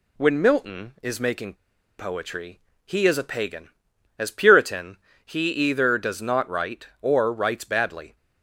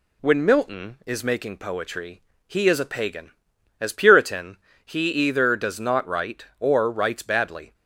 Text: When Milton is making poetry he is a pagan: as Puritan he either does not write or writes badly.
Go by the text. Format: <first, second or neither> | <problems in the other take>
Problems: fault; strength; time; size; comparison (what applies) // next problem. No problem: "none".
second | pauses between "making" and "poetry"; noticeable; at 1.5 s; 0.46 s long // pauses between "poetry" and "he"; slight; at 2.5 s; 0.26 s long; slight in the second // pauses between "Puritan" and "he"; slight; at 4.9 s; 0.28 s long; slight in the second